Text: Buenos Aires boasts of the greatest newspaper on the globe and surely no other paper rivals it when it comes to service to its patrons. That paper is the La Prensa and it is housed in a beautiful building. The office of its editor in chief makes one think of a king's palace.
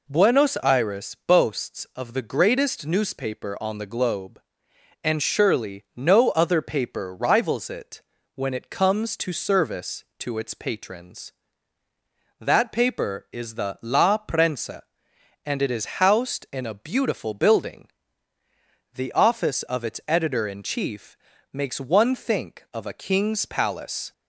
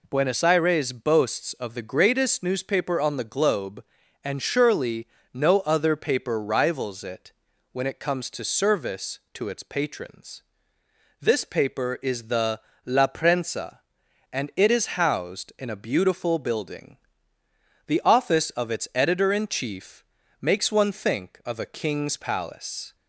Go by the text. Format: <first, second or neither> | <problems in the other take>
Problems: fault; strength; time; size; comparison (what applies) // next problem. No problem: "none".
first | pauses between "surely" and "no"; slight; at 5.0 s; 0.26 s long // pauses between "it" and "when"; at 7.3 s; 0.40 s long; slight in the first // says "This" for "That"; at 11.2 s // pauses between "the" and "La"; slight; at 12.6 s; 0.24 s long // pauses between "chief" and "makes"; slight; at 20.0 s; 0.36 s long; slight in the first